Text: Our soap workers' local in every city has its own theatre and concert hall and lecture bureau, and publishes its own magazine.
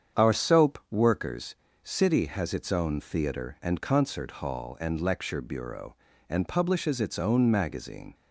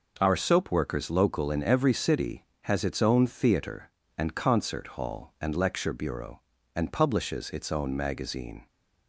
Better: second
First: starts louder than the rest; strong; until 1.3 s; 8 dB // skips "local in every"; at 1.6 s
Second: none

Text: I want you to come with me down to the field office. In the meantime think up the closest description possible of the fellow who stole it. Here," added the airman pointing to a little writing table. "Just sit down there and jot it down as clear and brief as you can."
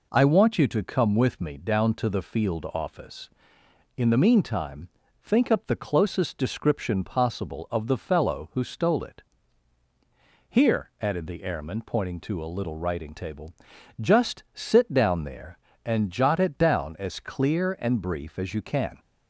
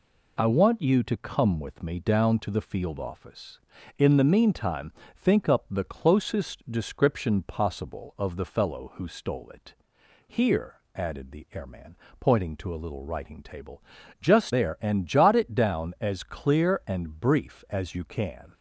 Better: first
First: pauses between "meantime" and "think"; slight; at 4.8 s; 0.34 s long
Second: pauses between "meantime" and "think"; slight; at 4.9 s; 0.24 s long // pauses between "airman" and "pointing"; slight; at 11.9 s; 0.24 s long // skips "sit down"; at 14.5 s

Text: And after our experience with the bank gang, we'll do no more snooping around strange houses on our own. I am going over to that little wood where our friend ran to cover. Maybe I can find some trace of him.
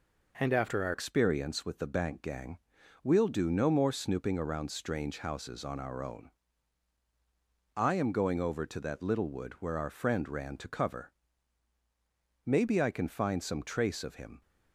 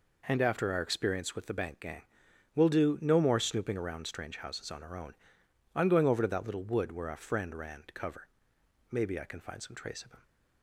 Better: second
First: changes voice at "experience"; from 0.9 s on; 13.5 s long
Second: none

